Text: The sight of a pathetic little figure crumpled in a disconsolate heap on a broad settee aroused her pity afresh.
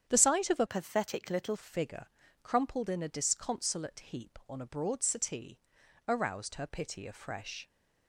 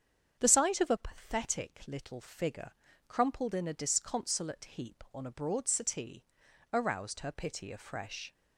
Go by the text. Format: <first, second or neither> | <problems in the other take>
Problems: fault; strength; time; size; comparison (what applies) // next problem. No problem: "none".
second | starts louder than the rest; strong; until 1.0 s; 8.5 dB; strong in the second // changes voice from "pathetic" to "little"; from 0.6 to 1.5 s; 0.9 s long // pauses between "figure" and "crumpled"; at 2.0 s; 0.38 s long; also in the second // pauses between "settee" and "aroused"; noticeable; at 5.6 s; 0.46 s long; noticeable in the second